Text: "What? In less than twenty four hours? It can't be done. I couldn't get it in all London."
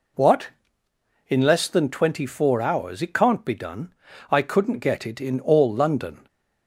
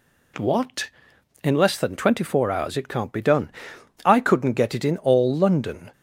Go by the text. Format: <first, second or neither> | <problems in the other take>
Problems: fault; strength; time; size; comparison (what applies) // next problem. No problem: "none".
neither | none